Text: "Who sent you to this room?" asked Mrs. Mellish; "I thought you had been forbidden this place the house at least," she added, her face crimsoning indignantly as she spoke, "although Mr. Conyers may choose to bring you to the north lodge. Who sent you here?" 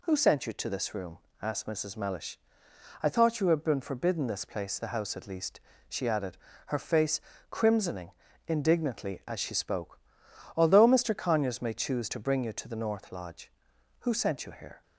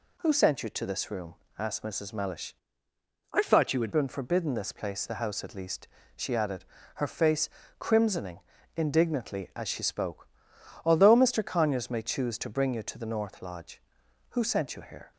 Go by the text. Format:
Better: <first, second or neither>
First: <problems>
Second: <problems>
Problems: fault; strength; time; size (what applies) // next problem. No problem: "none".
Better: first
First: pauses between "face" and "crimsoning"; slight; at 7.1 s; 0.30 s long // pauses between "crimsoning" and "indignantly"; slight; at 8.1 s; 0.36 s long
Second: changes voice from "I" to "had"; from 3.3 to 3.9 s; 0.6 s long // pauses between "face" and "crimsoning"; slight; at 7.4 s; 0.30 s long // pauses between "crimsoning" and "indignantly"; slight; at 8.4 s; 0.36 s long